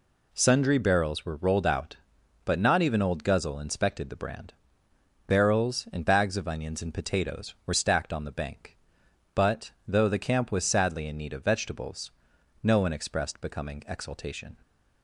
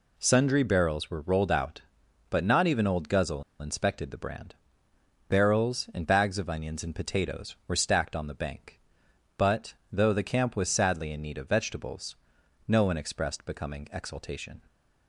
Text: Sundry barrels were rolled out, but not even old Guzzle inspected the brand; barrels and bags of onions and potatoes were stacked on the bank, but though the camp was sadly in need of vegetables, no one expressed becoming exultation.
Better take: first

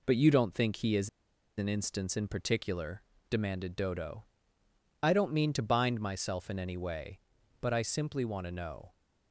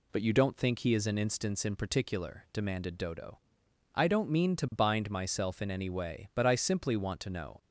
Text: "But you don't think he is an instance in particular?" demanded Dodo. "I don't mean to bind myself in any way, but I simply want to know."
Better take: second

